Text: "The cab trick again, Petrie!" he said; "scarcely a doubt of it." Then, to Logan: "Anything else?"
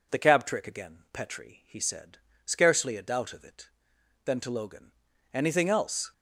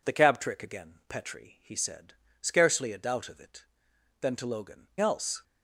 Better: first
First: none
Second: skips "Anything"; at 4.9 s

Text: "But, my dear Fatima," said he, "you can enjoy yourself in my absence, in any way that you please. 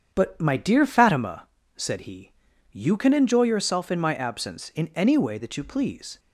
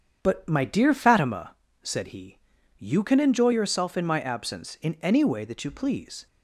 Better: neither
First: starts louder than the rest; strong; until 1.1 s; 8 dB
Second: starts louder than the rest; strong; until 1.2 s; 8 dB

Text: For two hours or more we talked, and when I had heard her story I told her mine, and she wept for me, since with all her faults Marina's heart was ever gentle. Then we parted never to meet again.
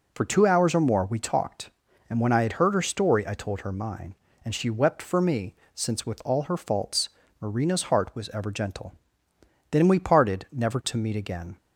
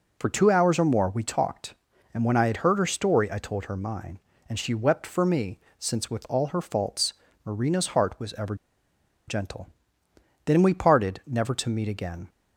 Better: first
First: pauses between "faults" and "Marina's"; slight; at 7.1 s; 0.30 s long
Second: pauses between "faults" and "Marina's"; slight; at 7.1 s; 0.30 s long // pauses between "ever" and "gentle"; noticeable; at 8.5 s; 0.73 s long

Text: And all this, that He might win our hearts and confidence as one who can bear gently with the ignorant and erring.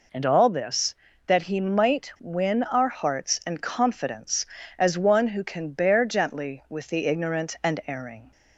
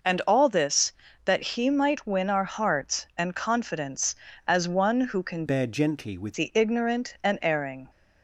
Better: first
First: none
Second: changes voice from "bear" to "with"; from 5.4 to 6.3 s; 0.9 s long

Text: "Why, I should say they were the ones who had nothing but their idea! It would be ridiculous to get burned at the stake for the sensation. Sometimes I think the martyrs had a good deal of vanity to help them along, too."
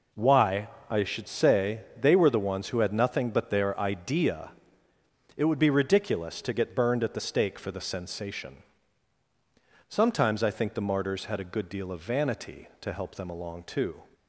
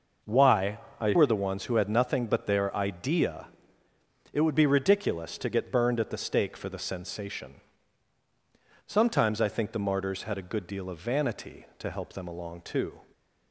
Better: first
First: none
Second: skips "should say they"; at 1.1 s

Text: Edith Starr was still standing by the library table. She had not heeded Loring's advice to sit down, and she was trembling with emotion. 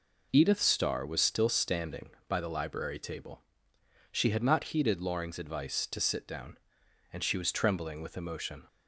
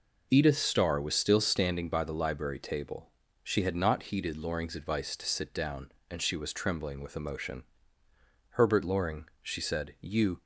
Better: first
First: none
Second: goes on to say "Herbert Loring she said you"; strong; from 8.5 s on; 1.9 s long

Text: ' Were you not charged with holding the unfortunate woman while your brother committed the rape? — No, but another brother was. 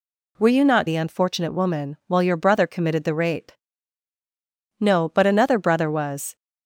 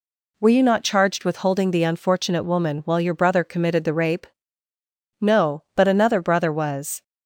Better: second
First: skips "charged with holding"; at 0.8 s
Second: none

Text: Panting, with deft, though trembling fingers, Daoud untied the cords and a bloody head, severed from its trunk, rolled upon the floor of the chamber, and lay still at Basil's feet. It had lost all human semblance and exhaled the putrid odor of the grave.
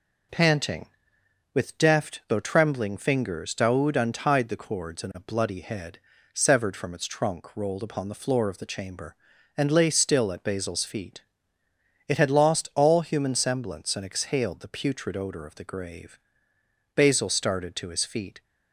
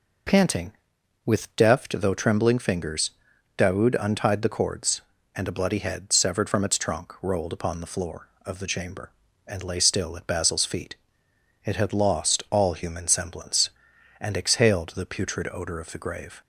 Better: second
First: goes on to say "Basil started to his feet"; from 16.9 s on; 1.4 s long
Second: none

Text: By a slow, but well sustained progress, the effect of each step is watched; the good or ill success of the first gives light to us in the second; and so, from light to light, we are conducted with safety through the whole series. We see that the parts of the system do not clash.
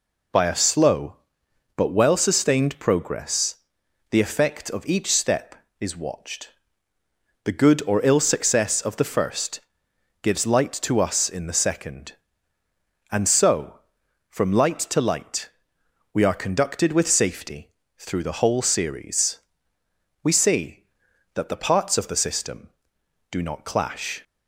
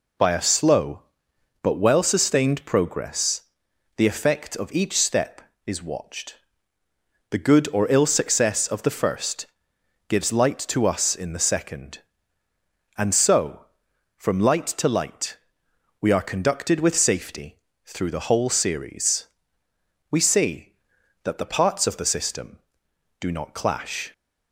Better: neither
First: pauses between "first" and "gives"; noticeable; at 9.5 s; 0.64 s long // pauses between "safety" and "through"; slight; at 17.7 s; 0.26 s long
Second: pauses between "first" and "gives"; noticeable; at 9.4 s; 0.64 s long // pauses between "safety" and "through"; slight; at 17.6 s; 0.26 s long

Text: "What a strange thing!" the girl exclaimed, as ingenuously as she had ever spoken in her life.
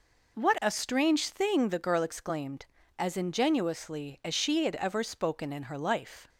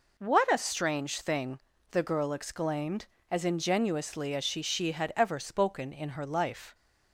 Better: first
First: none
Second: says "she" twice; at 4.6 s

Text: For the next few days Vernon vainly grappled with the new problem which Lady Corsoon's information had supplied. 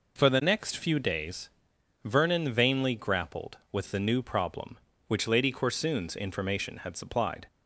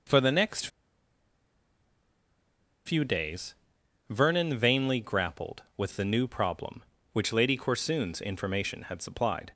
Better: first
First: pauses between "days" and "Vernon"; noticeable; at 1.4 s; 0.56 s long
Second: pauses between "next" and "few"; strong; at 0.6 s; 2.1 s long // pauses between "days" and "Vernon"; noticeable; at 3.5 s; 0.56 s long

